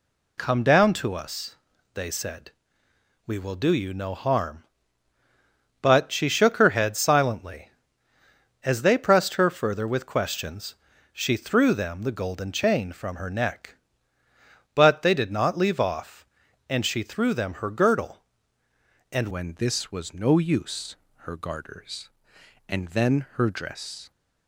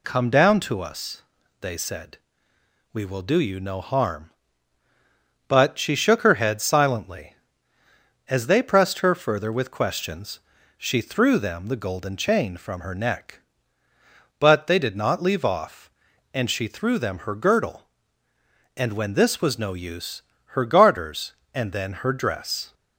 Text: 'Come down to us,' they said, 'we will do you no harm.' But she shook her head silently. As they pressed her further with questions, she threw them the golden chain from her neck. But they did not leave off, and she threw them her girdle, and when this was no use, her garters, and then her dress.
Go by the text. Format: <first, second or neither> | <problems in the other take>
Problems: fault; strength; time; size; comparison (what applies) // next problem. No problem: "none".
second | changes voice at "when"; from 19.3 s on; 4.8 s long